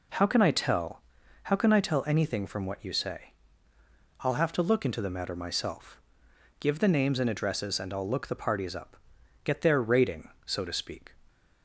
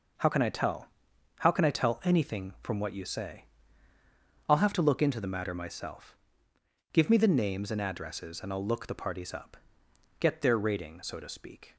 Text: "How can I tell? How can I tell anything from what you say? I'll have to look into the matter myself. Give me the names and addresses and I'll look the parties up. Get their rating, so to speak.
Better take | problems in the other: second | skips "me"; at 6.7 s

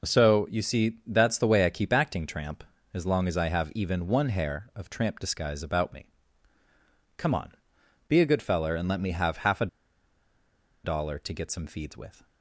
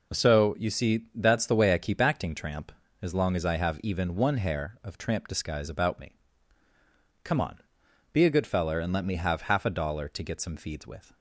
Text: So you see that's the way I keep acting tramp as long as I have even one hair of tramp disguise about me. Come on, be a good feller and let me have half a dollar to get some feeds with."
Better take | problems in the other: second | pauses between "a" and "dollar"; at 9.6 s; 1.1 s long

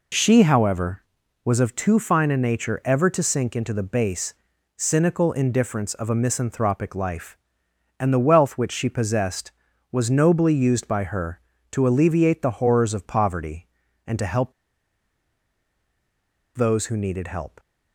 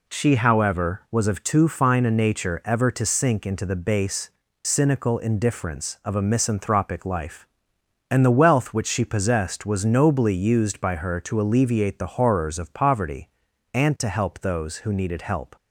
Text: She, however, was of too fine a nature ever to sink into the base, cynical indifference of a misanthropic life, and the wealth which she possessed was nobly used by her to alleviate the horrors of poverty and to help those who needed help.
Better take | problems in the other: second | pauses between "help" and "those"; strong; at 14.5 s; 2.0 s long

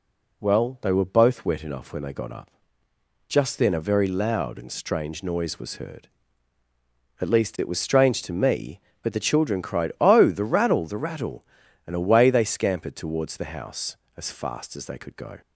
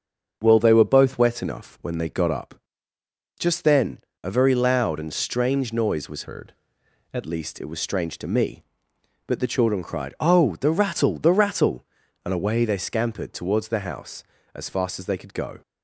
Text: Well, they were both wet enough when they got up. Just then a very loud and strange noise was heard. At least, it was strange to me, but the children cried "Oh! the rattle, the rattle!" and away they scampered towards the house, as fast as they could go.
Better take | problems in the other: first | starts louder than the rest; until 1.4 s; 6.5 dB // pauses between "then" and "a"; slight; at 4.0 s; 0.22 s long // changes voice from "heard" to "At"; from 6.2 to 7.2 s; 1.0 s long

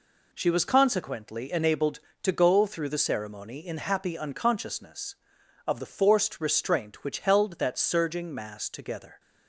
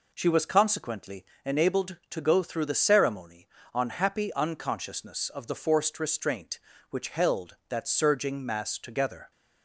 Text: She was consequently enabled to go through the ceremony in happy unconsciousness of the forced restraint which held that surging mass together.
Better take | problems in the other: first | pauses between "consequently" and "enabled"; slight; at 1.2 s; 0.20 s long // says "on" for "in"; at 3.7 s

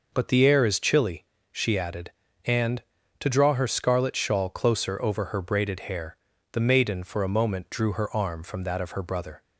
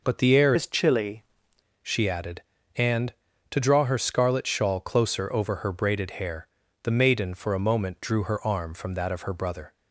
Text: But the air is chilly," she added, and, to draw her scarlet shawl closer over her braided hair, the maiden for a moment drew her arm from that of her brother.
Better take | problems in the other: first | changes voice from "is" to "chilly"; from 0.5 to 1.2 s; 0.7 s long

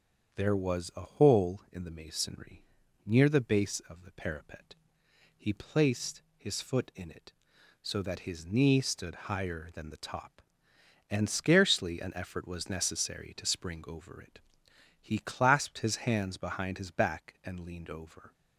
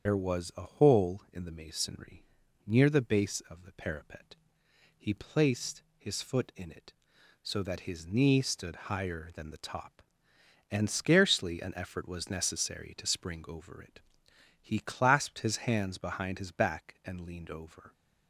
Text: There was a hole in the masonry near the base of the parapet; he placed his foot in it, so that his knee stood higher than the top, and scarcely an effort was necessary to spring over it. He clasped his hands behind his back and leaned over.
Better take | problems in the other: first | loses the start of "There"; at 0.0 s; 105 ms // starts louder than the rest; strong; until 1.1 s; 7.5 dB; strong in the first // pauses between "masonry" and "near"; at 2.2 s; 0.42 s long; also in the first // pauses between "placed" and "his"; slight; at 5.8 s; 0.16 s long; slight in the first

